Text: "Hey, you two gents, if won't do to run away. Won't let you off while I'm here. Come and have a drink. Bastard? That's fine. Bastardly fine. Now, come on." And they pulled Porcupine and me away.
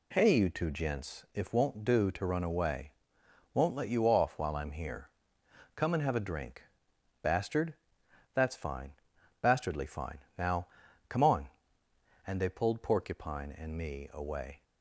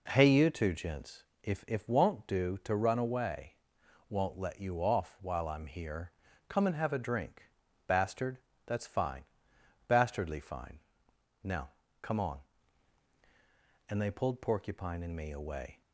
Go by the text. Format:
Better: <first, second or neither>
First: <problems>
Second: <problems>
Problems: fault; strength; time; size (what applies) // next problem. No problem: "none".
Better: first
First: none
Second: says "if" twice; at 1.6 s